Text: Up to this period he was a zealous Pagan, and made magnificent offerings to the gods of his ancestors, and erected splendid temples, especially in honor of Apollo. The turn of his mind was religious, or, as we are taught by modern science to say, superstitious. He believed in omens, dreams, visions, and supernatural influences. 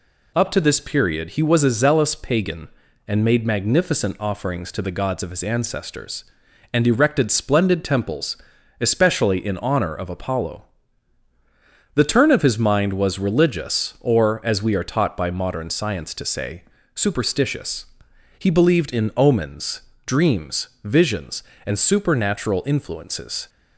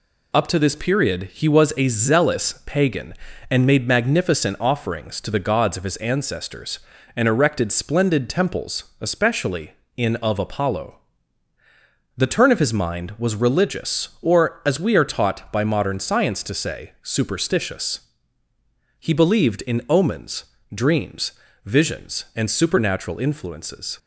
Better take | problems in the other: first | skips "honor"; at 10.1 s

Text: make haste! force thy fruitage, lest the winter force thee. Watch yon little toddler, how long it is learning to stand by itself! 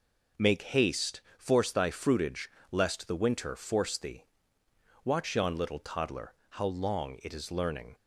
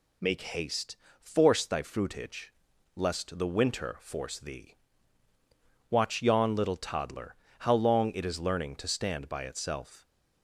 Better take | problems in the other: second | stops before "to stand by itself"; at 7.9 s

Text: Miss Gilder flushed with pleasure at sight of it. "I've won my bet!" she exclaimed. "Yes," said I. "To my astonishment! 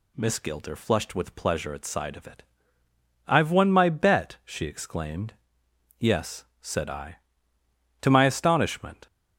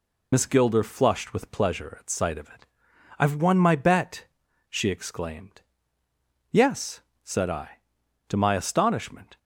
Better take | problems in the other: first | loses the start of "Miss"; at 0.3 s; 50 ms

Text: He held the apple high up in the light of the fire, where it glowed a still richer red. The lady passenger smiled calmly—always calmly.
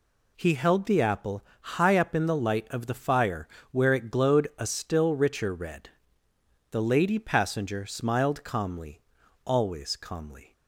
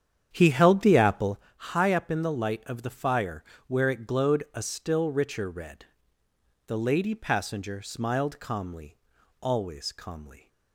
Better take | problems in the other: first | starts louder than the rest; strong; until 1.5 s; 8.5 dB // pauses between "apple" and "high"; slight; at 1.3 s; 0.18 s long; slight in the first

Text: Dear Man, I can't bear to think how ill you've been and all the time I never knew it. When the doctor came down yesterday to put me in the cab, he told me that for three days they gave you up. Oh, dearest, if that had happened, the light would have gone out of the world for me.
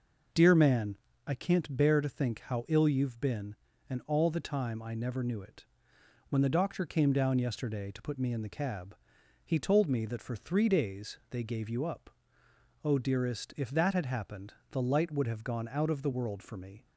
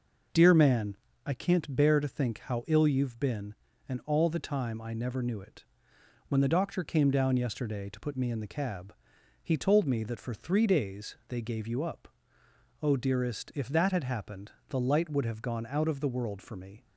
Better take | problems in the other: neither | none

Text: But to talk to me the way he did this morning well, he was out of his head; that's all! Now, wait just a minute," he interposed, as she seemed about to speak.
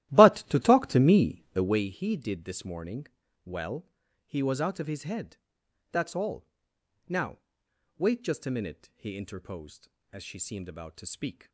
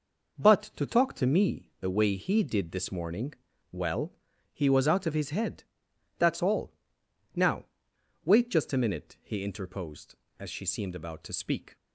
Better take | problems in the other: second | starts louder than the rest; strong; until 1.9 s; 14.5 dB // pauses between "morning" and "well"; at 3.0 s; 0.40 s long; also in the second

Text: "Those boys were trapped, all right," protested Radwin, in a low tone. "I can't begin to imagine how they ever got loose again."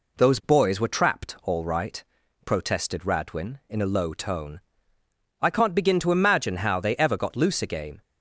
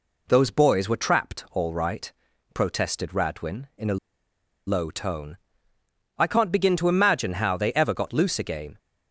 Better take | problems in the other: first | pauses between "a" and "low"; noticeable; at 3.9 s; 0.71 s long

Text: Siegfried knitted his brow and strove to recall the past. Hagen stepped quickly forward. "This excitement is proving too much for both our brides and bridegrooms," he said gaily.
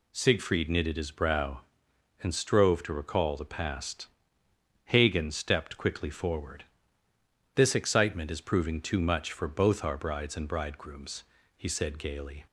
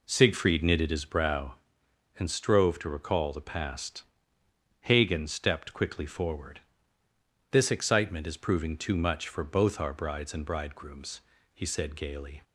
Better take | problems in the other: first | starts louder than the rest; until 1.2 s; 3.5 dB

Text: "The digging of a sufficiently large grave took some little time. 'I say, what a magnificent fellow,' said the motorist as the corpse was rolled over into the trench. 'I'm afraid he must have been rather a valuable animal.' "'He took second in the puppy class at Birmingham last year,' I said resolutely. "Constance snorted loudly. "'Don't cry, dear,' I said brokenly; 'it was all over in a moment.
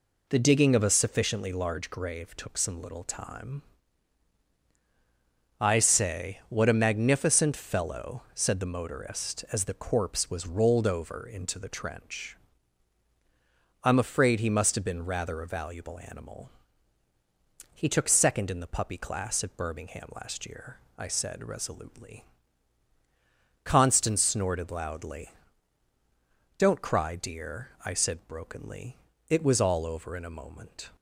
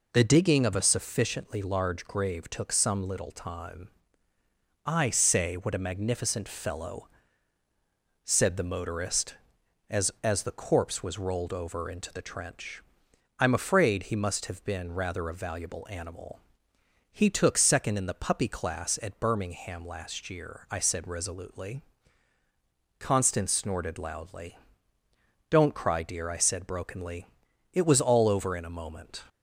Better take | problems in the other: first | says "as" twice; at 10.2 s

